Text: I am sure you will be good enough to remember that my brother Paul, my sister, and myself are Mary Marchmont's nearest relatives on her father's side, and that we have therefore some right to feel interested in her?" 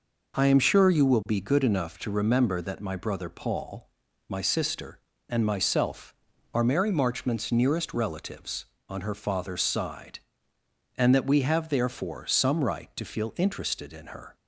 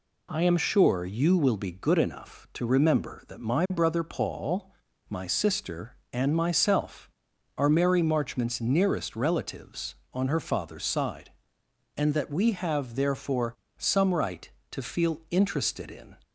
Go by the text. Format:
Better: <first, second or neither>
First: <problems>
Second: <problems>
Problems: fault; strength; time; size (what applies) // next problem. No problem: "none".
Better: first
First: none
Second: pauses between "therefore" and "some"; slight; at 13.5 s; 0.24 s long // stops before "her"; at 16.2 s